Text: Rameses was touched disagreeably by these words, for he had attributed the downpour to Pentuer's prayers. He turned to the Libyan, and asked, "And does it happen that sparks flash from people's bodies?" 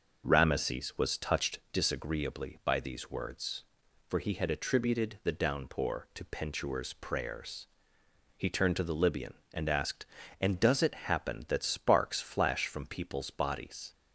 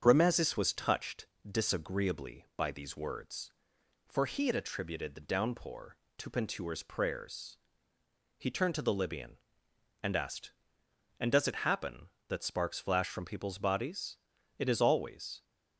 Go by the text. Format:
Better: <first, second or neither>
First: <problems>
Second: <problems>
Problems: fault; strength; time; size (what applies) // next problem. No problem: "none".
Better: first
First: none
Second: starts louder than the rest; strong; until 1.0 s; 7.5 dB // pauses between "touched" and "disagreeably"; slight; at 1.2 s; 0.22 s long // goes on to say "It is always"; noticeable; from 14.5 s on; 0.86 s long